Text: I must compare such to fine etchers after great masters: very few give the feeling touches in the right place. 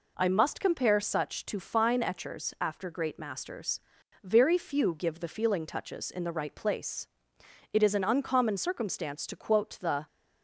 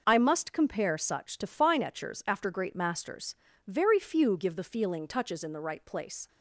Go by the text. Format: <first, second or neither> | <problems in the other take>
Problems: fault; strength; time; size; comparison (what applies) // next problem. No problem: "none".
second | goes on to say "It is an uncommon circumstance to quote the"; strong; from 7.7 s on; 2.3 s long